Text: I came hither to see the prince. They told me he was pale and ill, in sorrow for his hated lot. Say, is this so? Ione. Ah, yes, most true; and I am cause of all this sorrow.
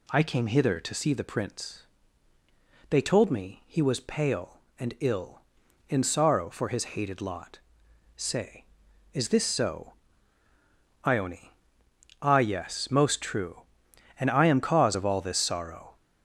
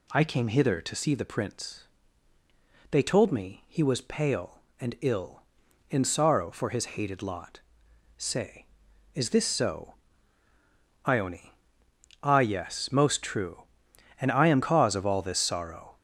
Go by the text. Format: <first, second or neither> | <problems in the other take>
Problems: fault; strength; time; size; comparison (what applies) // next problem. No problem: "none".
neither | none